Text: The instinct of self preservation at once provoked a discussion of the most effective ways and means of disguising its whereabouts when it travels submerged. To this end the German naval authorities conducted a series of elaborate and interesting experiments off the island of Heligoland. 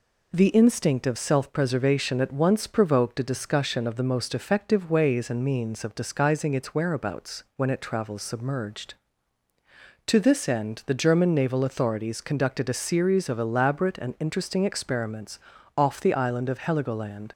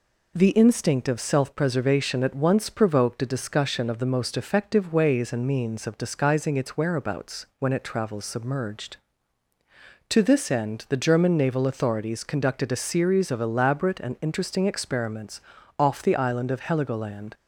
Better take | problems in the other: neither | pauses between "experiments" and "off"; the same in both

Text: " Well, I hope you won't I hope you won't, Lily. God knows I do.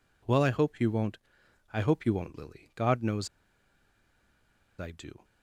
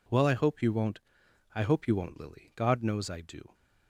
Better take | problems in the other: second | pauses between "won't" and "I"; noticeable; at 1.1 s; 0.56 s long; noticeable in the second // pauses between "knows" and "I"; strong; at 3.2 s; 1.5 s long

